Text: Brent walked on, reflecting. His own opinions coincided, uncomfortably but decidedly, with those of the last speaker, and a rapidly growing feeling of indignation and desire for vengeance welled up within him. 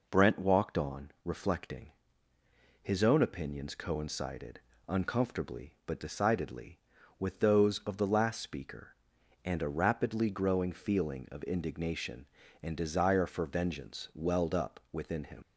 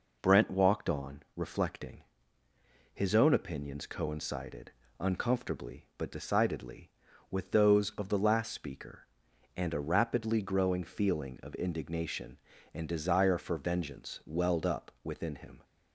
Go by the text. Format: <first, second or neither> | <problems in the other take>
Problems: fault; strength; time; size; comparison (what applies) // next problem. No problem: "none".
second | leaves "him" unfinished; at 15.4 s; 95 ms